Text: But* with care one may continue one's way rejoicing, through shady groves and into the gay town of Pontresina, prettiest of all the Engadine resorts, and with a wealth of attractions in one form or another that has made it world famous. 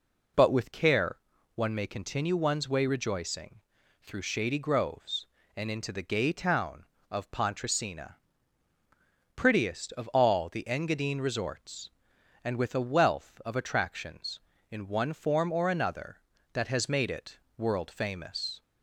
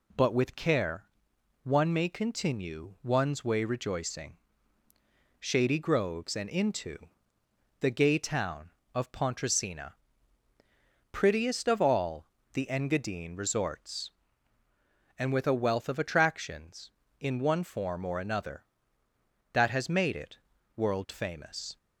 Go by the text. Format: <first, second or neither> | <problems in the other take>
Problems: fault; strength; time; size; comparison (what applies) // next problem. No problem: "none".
first | pauses between "care" and "one"; noticeable; at 1.0 s; 0.58 s long; slight in the first // skips "through"; at 4.8 s // pauses between "into" and "the"; noticeable; at 6.9 s; 0.82 s long // pauses between "all" and "the"; slight; at 12.2 s; 0.28 s long // pauses between "it" and "world"; at 20.3 s; 0.38 s long; slight in the first